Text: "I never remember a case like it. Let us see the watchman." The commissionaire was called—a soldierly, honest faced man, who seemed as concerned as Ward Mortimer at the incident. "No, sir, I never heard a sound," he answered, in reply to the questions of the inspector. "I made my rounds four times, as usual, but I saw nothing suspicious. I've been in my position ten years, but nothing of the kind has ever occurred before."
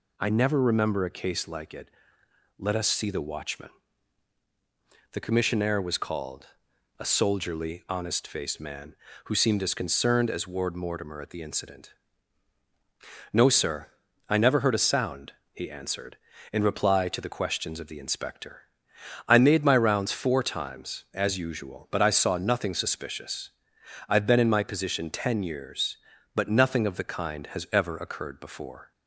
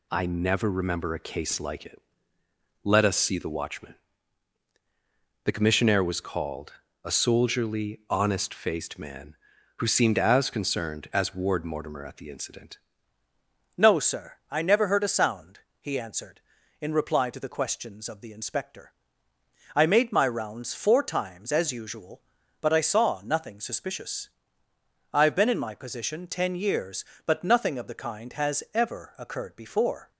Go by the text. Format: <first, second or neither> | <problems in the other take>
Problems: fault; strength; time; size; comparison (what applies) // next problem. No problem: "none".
first | changes voice at "No"; from 13.7 s on; 16.4 s long